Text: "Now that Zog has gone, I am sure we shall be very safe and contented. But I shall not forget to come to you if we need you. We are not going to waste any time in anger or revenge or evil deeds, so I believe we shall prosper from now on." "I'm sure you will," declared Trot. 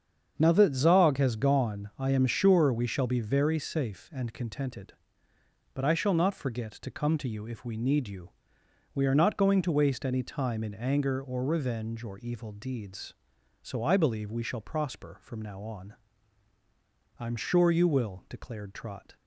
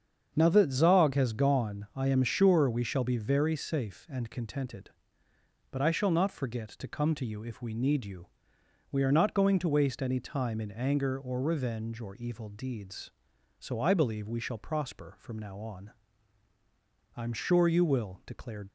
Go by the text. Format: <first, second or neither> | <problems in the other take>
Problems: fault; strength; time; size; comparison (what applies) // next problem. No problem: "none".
first | starts louder than the rest; strong; until 1.3 s; 7.5 dB; strong in the first // stops before "Trot"; at 18.6 s